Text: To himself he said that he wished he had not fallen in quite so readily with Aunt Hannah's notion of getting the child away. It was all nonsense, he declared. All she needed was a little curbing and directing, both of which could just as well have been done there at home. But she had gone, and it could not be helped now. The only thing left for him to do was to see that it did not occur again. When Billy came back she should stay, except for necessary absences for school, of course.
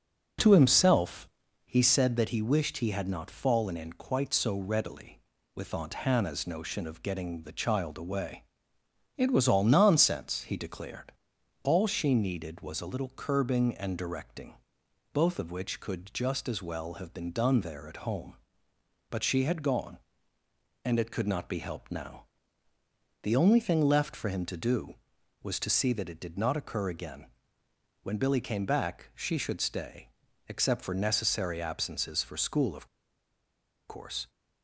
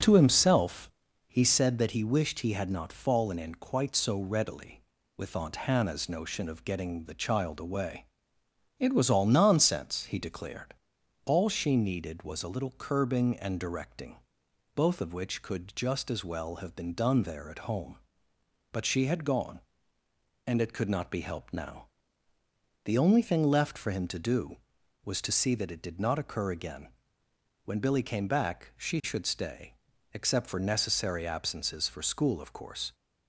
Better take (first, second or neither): second